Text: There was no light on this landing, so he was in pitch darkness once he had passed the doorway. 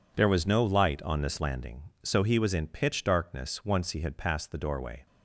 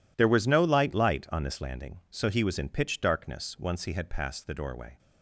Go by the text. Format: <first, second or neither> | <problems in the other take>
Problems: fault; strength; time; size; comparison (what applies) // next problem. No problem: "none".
first | says "light" twice; at 0.9 s